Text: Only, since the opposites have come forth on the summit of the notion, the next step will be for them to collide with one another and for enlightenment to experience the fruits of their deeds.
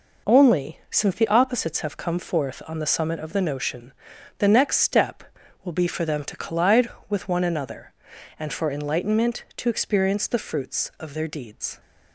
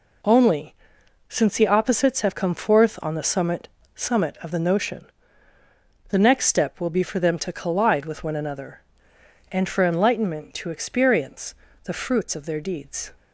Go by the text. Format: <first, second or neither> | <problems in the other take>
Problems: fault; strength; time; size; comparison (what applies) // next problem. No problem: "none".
first | says "summit" twice; at 3.9 s // pauses between "experience" and "the"; slight; at 11.5 s; 0.30 s long